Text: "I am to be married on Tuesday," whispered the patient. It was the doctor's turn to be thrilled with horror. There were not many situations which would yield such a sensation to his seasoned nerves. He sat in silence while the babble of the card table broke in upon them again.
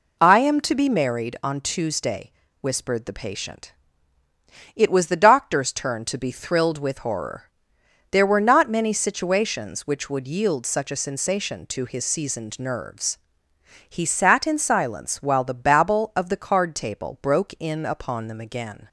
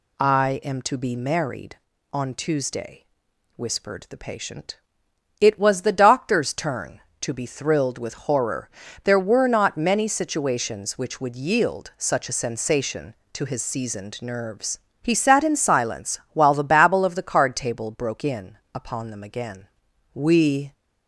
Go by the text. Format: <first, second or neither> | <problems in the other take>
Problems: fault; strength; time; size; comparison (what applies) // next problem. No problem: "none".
first | pauses between "in" and "upon"; slight; at 18.5 s; 0.16 s long // goes on to say "We"; from 20.1 s on; 0.60 s long